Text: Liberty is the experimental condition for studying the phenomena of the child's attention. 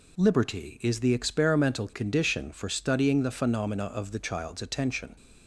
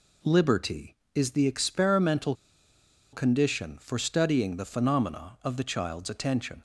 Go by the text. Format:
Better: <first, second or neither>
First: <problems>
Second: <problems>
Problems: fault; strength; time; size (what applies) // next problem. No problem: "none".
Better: first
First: none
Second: pauses between "experimental" and "condition"; noticeable; at 2.3 s; 0.79 s long